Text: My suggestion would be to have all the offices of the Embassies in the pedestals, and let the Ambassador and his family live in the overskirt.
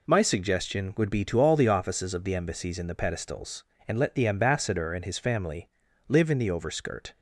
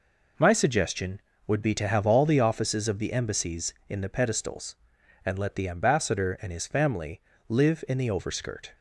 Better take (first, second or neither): second